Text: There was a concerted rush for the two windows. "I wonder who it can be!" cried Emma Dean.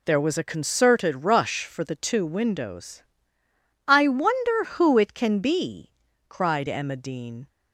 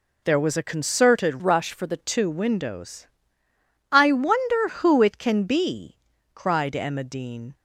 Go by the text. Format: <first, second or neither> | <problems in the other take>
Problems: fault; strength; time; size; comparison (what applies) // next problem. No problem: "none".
first | changes voice from "rush" to "the"; from 1.4 to 1.9 s; 0.5 s long